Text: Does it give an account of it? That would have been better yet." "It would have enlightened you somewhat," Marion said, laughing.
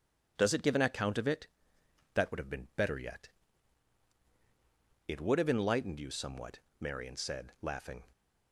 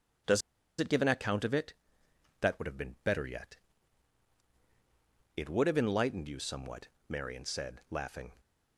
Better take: first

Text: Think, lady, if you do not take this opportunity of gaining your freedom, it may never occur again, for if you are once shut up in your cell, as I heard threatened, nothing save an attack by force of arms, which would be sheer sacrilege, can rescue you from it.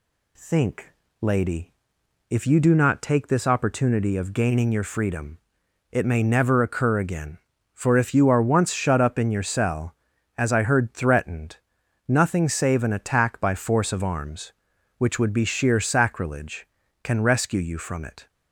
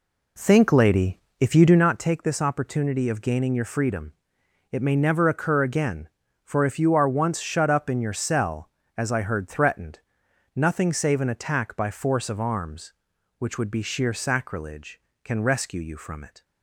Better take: first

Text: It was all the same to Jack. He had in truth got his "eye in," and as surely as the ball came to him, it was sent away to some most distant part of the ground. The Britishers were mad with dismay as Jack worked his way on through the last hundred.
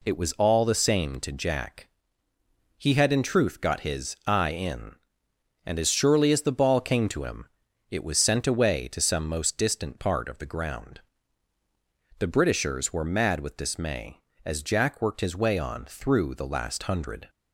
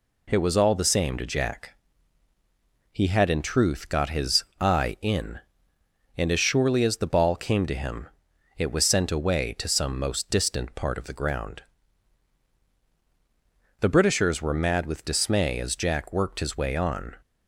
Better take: first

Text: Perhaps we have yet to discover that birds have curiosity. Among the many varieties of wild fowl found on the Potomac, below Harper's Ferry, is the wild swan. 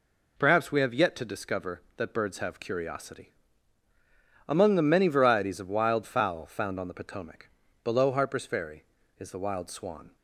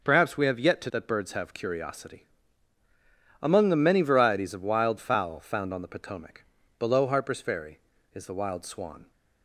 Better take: first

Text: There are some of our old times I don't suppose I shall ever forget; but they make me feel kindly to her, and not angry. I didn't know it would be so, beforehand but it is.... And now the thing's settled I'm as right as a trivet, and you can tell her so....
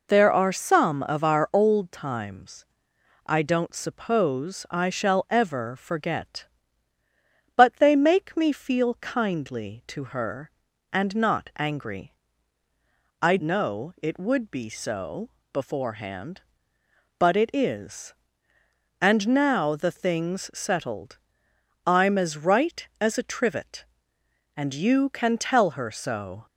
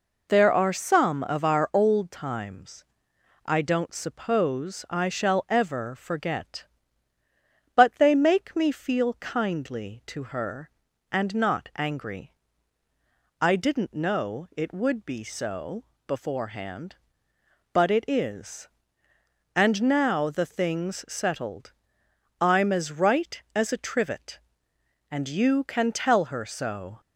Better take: second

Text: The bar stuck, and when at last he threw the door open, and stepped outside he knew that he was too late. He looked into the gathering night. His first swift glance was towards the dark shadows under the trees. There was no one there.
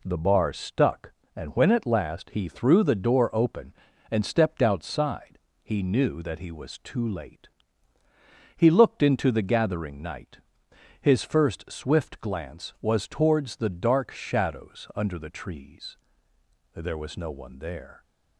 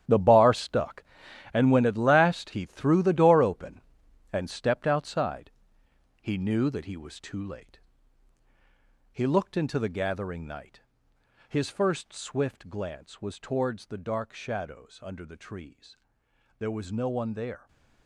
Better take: first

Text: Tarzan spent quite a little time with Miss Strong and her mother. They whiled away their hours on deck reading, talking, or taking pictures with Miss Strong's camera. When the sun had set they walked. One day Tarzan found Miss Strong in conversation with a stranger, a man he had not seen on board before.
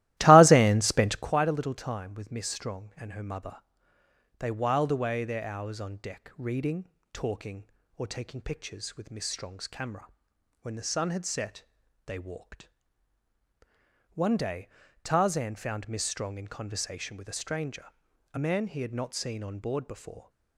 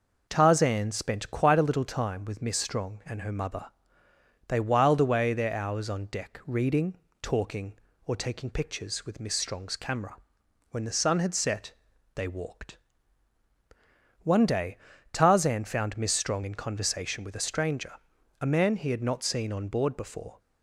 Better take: second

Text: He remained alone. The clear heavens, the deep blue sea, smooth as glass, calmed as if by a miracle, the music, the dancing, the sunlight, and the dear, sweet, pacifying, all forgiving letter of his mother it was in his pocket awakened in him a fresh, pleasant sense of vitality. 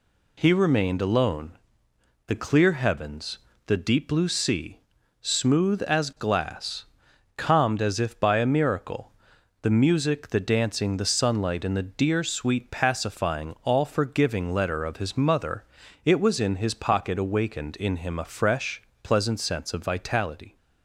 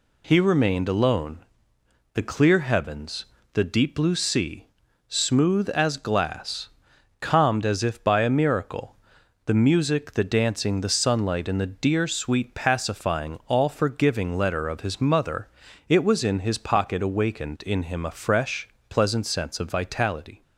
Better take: neither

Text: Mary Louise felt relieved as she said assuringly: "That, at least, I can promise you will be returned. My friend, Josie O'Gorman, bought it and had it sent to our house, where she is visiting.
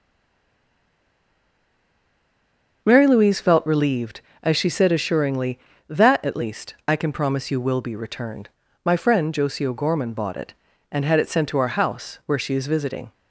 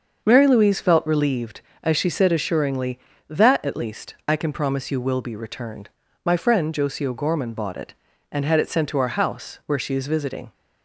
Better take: second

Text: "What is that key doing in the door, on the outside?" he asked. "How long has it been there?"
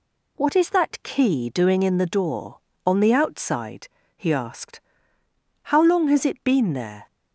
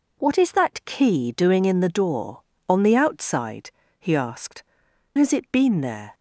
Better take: first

